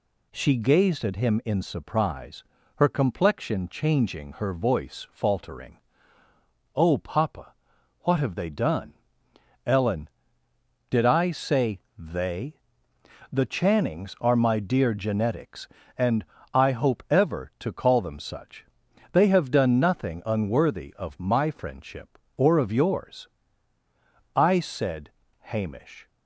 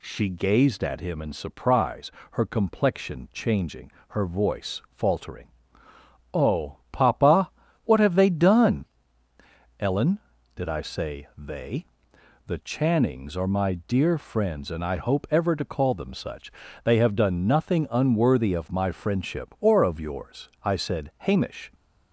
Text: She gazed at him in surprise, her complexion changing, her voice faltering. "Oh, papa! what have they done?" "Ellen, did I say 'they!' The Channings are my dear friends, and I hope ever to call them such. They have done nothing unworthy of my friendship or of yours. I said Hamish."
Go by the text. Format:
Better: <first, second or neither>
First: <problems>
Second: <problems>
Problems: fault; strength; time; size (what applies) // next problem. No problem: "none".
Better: second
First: pauses between "say" and "they"; slight; at 11.7 s; 0.18 s long // says "genetics" for "friends"; at 14.9 s // pauses between "and" and "I"; slight; at 16.2 s; 0.30 s long // pauses between "said" and "Hamish"; slight; at 25.0 s; 0.30 s long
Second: none